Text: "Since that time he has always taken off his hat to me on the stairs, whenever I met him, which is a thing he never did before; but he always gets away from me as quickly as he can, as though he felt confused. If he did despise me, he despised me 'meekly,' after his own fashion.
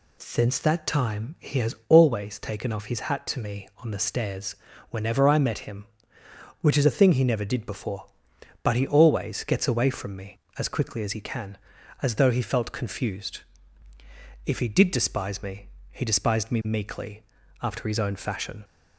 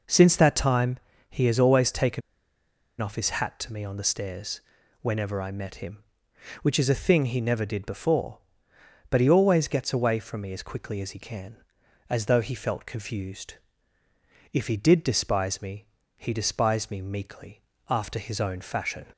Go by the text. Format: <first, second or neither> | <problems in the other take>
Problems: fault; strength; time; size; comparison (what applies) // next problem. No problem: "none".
first | pauses between "time" and "he"; slight; at 0.9 s; 0.30 s long // pauses between "taken" and "off"; noticeable; at 2.2 s; 0.79 s long